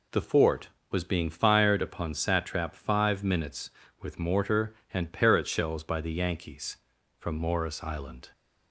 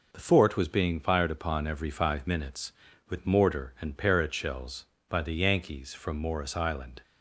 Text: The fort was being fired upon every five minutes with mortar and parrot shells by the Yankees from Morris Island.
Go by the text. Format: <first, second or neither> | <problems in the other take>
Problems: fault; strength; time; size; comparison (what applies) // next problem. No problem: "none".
second | says "satrap" for "every"; at 2.1 s